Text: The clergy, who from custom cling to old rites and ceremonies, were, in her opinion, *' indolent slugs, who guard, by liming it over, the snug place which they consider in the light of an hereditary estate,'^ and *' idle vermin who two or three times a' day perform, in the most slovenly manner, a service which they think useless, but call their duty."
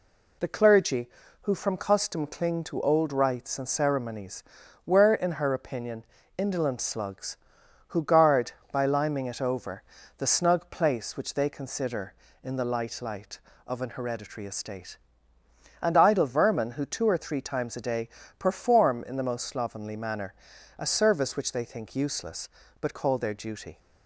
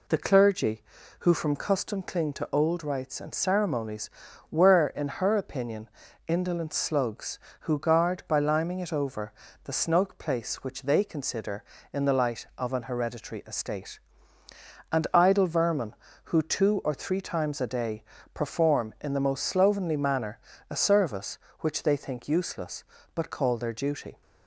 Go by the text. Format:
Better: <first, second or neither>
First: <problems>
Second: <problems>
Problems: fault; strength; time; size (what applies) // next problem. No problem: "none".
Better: second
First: says "light" twice; at 13.0 s // pauses between "day" and "perform"; slight; at 18.0 s; 0.28 s long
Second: pauses between "day" and "perform"; slight; at 18.0 s; 0.28 s long